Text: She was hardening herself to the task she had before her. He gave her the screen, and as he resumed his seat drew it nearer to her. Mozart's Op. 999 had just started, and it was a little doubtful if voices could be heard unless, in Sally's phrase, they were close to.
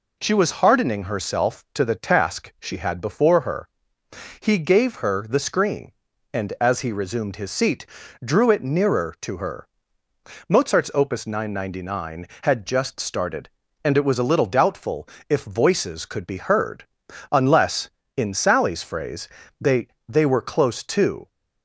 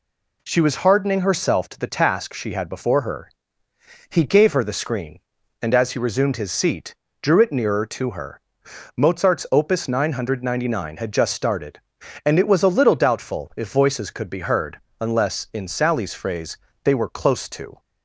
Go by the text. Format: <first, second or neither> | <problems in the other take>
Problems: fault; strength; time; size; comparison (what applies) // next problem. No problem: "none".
second | pauses between "seat" and "drew"; at 7.8 s; 0.38 s long; slight in the second // pauses between "doubtful" and "if"; slight; at 15.0 s; 0.22 s long // pauses between "heard" and "unless"; at 16.8 s; 0.44 s long; slight in the second // says "they" twice; at 20.0 s